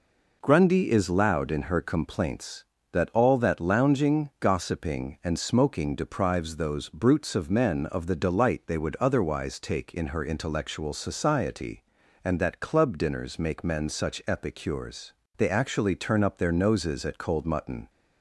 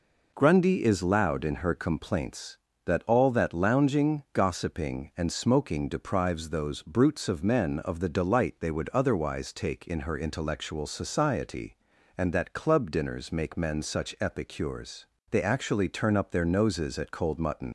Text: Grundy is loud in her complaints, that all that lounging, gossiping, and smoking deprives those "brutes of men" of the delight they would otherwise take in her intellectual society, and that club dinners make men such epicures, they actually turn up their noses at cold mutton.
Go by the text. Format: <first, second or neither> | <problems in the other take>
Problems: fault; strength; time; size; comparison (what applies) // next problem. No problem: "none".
first | leaves "mutton" unfinished; at 17.6 s; 100 ms